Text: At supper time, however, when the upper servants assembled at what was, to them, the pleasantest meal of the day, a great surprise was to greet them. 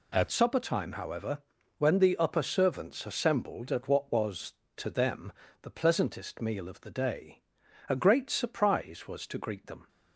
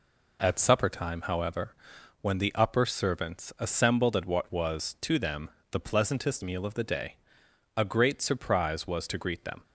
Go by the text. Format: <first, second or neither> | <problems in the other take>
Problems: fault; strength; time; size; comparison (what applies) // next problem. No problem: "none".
second | changes voice at "supper"; from 0.2 s on; 9.6 s long